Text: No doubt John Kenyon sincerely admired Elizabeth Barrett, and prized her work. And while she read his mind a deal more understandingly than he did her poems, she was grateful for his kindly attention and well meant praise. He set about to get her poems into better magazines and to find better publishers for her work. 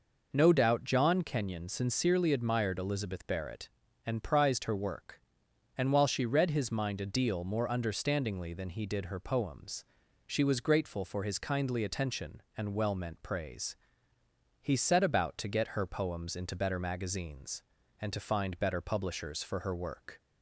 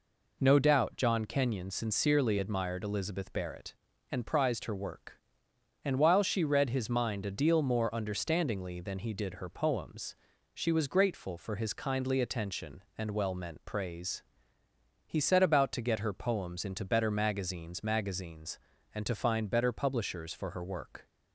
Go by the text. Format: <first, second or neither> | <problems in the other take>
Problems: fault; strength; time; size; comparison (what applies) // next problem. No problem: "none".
first | says "magazines" twice; at 17.8 s